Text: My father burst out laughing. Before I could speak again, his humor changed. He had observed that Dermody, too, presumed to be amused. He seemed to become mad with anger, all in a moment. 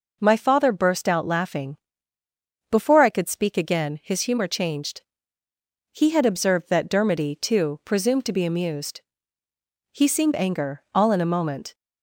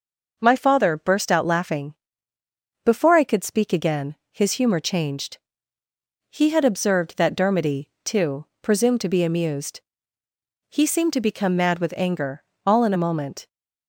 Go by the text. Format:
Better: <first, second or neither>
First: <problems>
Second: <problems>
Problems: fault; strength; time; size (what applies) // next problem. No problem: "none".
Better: second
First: skips "to become mad with"; at 10.3 s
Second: none